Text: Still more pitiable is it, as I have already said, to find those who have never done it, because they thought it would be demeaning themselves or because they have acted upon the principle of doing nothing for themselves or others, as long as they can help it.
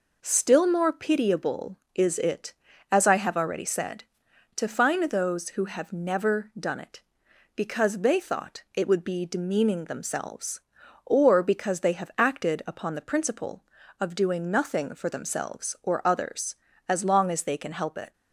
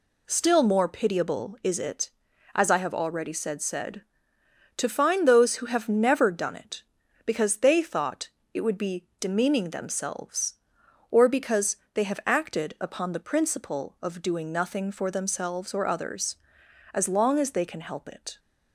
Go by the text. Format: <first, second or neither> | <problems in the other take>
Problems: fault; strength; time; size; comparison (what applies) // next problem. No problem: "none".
first | says "said" twice; at 3.6 s // pauses between "thought" and "it"; slight; at 8.2 s; 0.24 s long // pauses between "because" and "they"; slight; at 11.7 s; 0.16 s long